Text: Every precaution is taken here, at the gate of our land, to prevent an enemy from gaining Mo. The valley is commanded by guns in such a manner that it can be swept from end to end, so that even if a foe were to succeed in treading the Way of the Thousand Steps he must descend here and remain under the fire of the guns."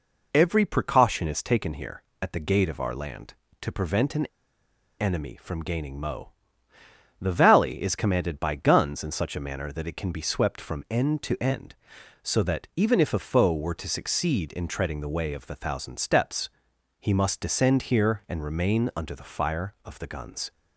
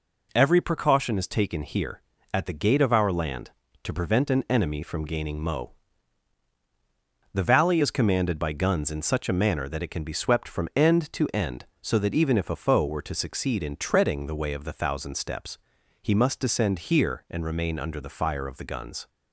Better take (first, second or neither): second